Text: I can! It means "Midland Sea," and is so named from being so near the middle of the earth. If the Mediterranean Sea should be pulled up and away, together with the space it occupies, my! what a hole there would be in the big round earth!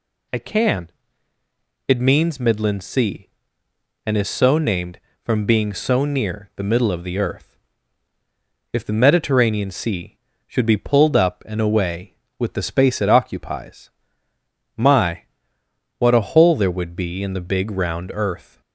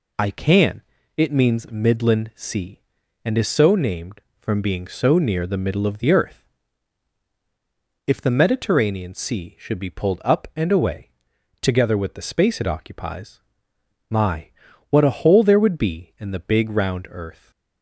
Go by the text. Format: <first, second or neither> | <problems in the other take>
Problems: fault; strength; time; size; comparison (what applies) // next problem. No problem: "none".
second | skips "together"; at 12.2 s